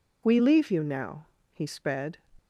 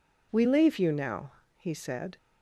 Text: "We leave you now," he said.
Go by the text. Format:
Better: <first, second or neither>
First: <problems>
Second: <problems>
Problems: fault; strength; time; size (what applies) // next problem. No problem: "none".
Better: second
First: says "sped" for "said"; at 1.6 s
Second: none